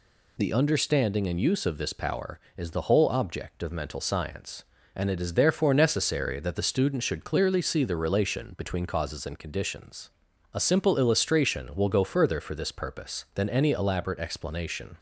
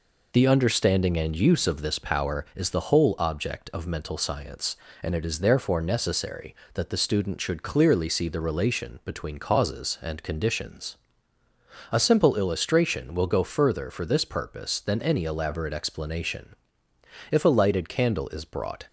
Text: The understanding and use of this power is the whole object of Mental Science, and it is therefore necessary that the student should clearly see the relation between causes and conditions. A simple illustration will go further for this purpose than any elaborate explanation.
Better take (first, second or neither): first